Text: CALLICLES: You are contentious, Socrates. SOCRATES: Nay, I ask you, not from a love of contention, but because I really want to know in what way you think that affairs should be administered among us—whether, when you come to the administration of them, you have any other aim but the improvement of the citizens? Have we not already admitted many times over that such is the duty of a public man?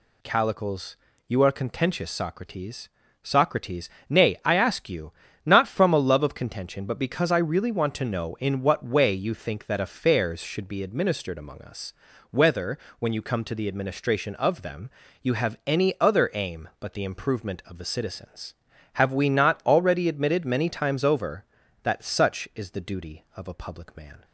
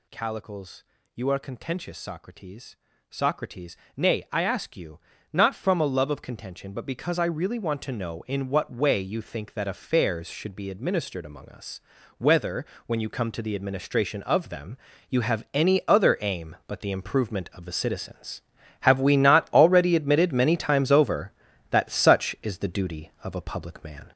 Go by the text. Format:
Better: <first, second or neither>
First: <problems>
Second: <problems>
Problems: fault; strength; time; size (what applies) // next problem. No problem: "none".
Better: first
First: none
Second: gets louder; noticeable; throughout; 6 dB